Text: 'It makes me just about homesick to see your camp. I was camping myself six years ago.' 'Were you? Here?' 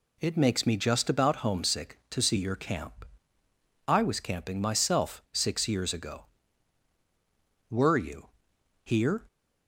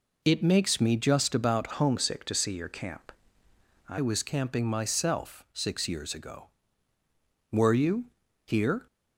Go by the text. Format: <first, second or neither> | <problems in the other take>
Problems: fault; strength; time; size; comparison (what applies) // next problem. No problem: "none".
first | changes voice from "homesick" to "I"; from 1.7 to 3.9 s; 2.2 s long